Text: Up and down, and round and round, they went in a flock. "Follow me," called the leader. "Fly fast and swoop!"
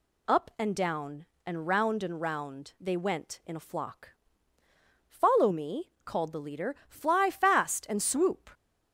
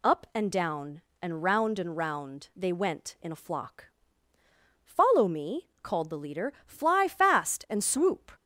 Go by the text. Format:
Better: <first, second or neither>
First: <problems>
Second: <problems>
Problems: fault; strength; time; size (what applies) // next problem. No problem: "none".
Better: neither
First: none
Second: none